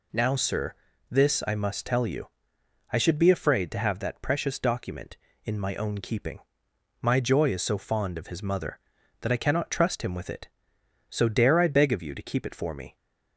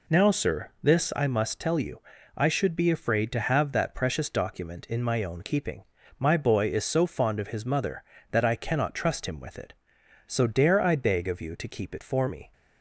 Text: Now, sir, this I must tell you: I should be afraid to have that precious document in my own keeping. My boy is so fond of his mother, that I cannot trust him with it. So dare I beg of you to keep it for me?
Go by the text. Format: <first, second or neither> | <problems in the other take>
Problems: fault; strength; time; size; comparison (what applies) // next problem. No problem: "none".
second | says "joy" for "boy"; at 7.1 s